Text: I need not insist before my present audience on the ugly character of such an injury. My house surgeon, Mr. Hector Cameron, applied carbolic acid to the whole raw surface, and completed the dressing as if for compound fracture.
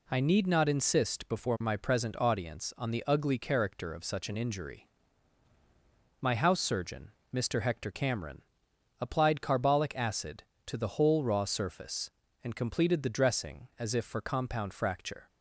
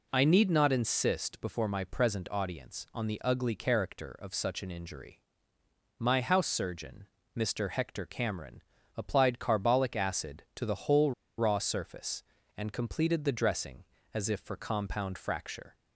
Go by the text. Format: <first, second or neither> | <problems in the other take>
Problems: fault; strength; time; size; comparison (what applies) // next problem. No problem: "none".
first | pauses between "whole" and "raw"; slight; at 11.1 s; 0.25 s long